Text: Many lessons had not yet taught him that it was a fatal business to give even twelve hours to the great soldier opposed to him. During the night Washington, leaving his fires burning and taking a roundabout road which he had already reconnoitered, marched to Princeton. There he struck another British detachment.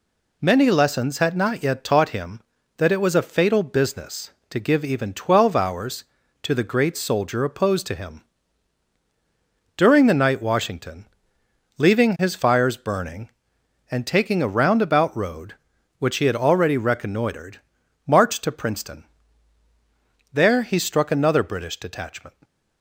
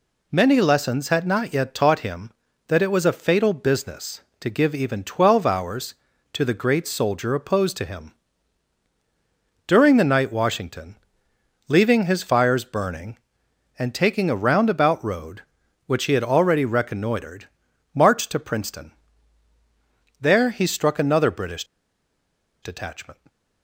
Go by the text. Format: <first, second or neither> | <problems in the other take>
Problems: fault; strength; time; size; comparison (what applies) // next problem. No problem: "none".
first | pauses between "British" and "detachment"; at 21.6 s; 0.99 s long